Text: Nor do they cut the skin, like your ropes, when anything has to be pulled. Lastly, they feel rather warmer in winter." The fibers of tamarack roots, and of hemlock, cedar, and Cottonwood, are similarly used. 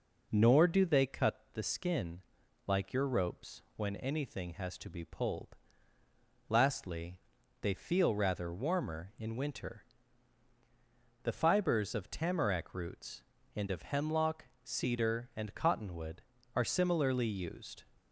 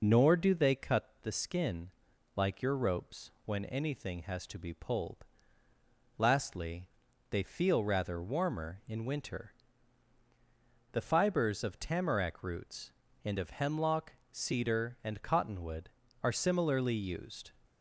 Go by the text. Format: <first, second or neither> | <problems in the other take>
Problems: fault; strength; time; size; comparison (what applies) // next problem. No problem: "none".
first | loses the start of "Nor"; at 0.0 s; 30 ms